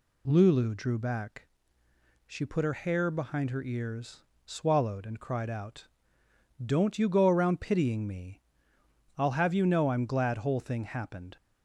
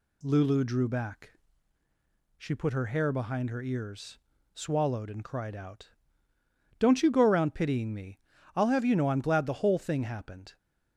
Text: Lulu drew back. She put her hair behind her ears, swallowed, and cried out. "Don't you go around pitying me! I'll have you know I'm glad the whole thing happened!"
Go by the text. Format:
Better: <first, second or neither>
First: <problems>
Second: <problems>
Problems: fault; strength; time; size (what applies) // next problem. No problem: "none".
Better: second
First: skips "the"; at 10.3 s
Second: none